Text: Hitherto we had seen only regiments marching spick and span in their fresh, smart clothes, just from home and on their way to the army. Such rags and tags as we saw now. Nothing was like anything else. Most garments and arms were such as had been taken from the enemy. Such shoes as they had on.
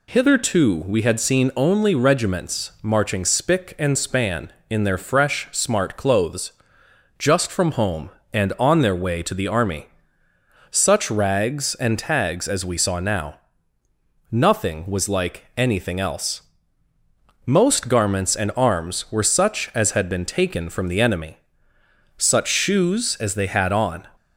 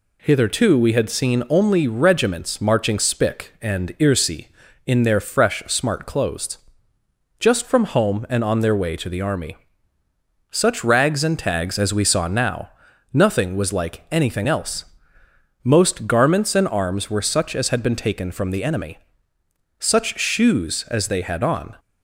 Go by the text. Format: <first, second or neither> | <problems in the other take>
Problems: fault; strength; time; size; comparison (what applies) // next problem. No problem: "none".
first | says "irsi" for "span"; at 3.9 s